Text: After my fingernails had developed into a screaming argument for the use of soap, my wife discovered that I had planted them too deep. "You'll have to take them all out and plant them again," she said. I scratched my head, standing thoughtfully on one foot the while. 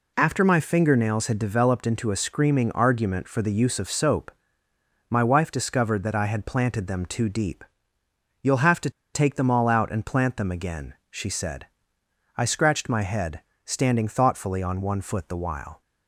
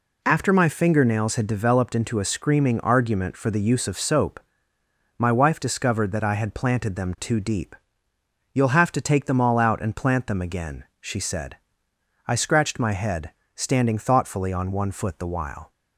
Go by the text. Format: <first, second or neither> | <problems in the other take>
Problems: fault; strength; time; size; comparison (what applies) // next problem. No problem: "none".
second | pauses between "to" and "take"; slight; at 8.8 s; 0.23 s long